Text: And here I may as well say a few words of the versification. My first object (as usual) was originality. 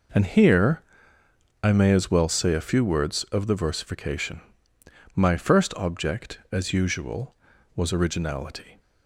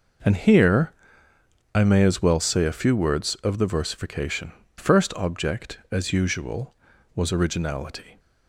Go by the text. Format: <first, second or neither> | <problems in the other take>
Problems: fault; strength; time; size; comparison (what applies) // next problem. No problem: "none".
first | pauses between "here" and "I"; noticeable; at 0.9 s; 0.80 s long; noticeable in the first // skips "My"; at 4.6 s